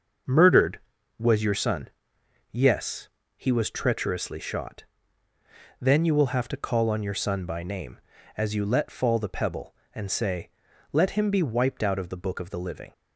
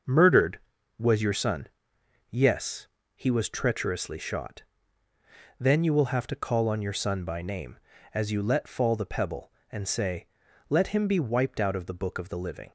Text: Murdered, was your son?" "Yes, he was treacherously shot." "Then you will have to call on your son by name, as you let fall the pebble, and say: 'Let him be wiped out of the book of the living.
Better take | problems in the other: neither | starts louder than the rest; the same in both

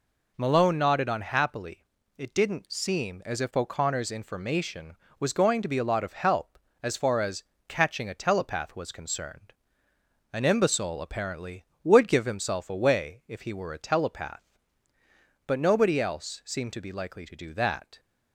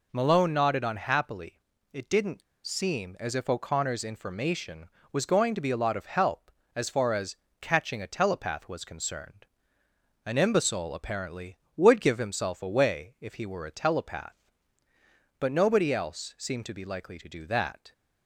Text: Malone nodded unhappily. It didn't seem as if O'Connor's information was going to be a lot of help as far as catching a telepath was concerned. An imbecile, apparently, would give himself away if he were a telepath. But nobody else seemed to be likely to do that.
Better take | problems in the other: first | pauses between "didn't" and "seem"; slight; at 2.4 s; 0.21 s long // pauses between "as" and "catching"; slight; at 7.3 s; 0.24 s long; slight in the first

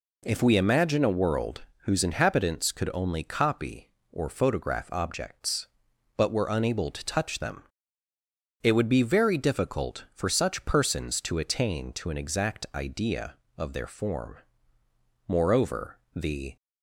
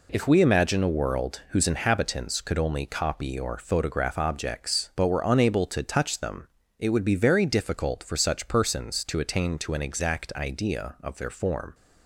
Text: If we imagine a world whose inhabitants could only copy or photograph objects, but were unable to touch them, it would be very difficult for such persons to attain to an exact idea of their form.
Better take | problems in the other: second | pauses between "world" and "whose"; slight; at 1.6 s; 0.18 s long // goes on to say "Moreover the"; noticeable; from 15.2 s on; 1.2 s long

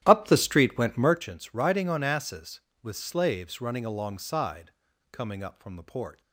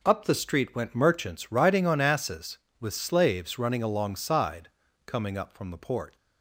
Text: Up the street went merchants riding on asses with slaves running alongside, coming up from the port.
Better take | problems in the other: second | starts louder than the rest; strong; until 1.2 s; 12 dB

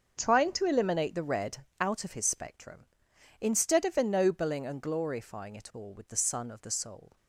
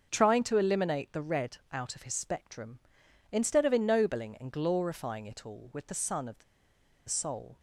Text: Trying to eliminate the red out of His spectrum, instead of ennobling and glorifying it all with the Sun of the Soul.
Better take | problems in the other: first | starts louder than the rest; until 1.1 s; 7 dB; also in the first // pauses between "red" and "out"; slight; at 1.5 s; 0.16 s long; slight in the first // pauses between "the" and "Soul"; noticeable; at 6.4 s; 0.65 s long

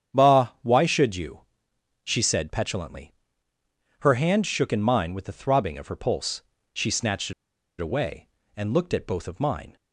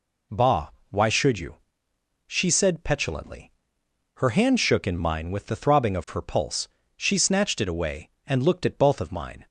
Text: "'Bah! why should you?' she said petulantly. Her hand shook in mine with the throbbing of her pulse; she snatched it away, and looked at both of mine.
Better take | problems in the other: second | starts louder than the rest; strong; until 1.2 s; 8.5 dB // pauses between "it" and "away"; noticeable; at 7.3 s; 0.48 s long

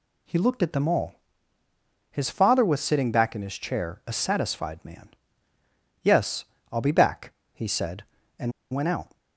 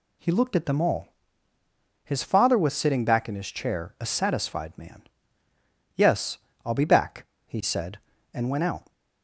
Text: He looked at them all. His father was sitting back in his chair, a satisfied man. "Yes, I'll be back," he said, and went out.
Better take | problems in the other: second | pauses between "and" and "went"; slight; at 8.5 s; 0.20 s long

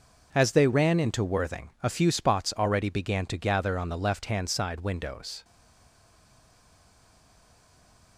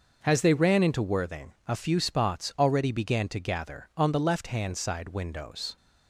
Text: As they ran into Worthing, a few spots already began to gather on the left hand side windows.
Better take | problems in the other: second | stays silent after the last word; strong; from 5.4 s on; 2.7 s long

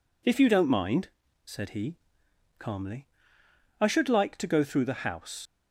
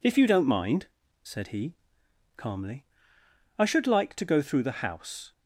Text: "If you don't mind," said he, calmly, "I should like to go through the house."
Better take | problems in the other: second | leaves "house" unfinished; at 5.4 s; 85 ms

